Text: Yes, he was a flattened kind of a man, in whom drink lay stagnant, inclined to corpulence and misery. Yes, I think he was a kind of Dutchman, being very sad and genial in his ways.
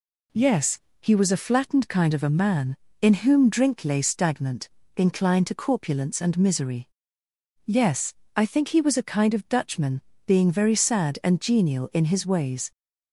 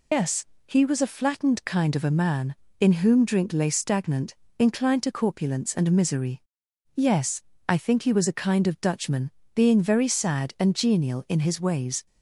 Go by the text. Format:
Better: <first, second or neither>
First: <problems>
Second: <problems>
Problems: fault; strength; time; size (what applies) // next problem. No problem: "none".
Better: first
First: none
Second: loses the start of "Yes"; at 0.1 s; 165 ms